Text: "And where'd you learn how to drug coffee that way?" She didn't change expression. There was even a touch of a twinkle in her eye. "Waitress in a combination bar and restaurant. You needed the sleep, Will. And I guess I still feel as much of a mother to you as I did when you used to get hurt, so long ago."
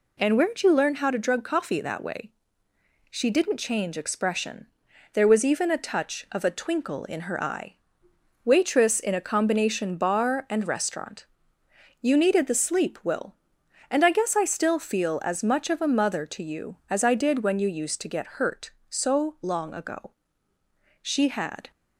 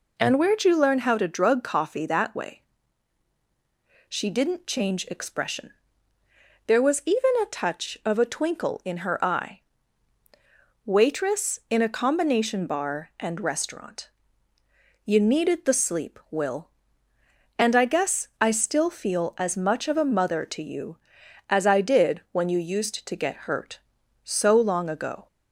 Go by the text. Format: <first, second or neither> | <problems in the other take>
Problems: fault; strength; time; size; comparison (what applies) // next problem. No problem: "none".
second | goes on to say "She had"; noticeable; from 21.0 s on; 0.70 s long